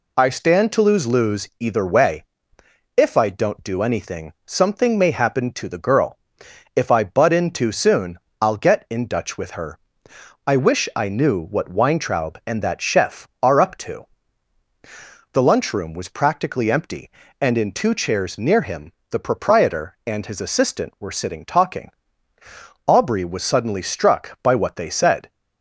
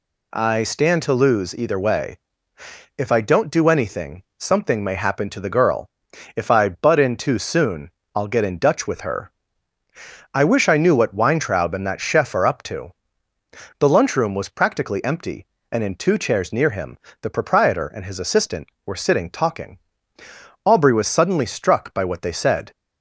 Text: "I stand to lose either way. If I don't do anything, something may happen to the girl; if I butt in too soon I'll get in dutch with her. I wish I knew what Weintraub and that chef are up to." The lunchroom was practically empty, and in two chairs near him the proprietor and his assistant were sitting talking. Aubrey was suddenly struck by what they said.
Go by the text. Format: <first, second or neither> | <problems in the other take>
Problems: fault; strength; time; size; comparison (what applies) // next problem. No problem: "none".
second | says "lose" twice; at 1.0 s // pauses between "soon" and "I'll"; slight; at 8.1 s; 0.22 s long; slight in the second // pauses between "him" and "the"; slight; at 18.9 s; 0.18 s long; slight in the second